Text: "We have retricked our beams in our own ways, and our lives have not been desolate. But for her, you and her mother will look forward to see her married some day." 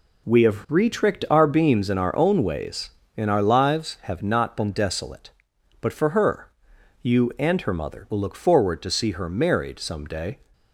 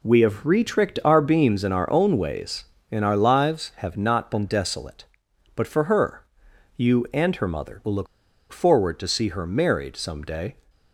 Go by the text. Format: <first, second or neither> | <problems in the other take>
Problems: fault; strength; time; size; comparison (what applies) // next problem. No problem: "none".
first | pauses between "look" and "forward"; at 8.0 s; 0.44 s long